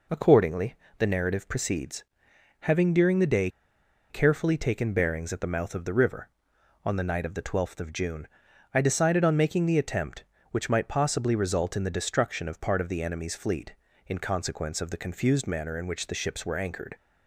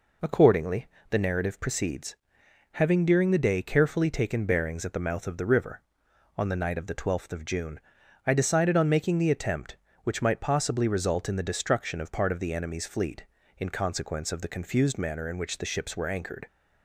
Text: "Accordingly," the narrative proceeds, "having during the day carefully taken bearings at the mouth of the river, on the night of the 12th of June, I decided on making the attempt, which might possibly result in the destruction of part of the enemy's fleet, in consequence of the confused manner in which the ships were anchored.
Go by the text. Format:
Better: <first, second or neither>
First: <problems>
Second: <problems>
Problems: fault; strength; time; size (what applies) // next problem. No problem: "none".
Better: second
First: pauses between "day" and "carefully"; noticeable; at 3.4 s; 0.61 s long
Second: none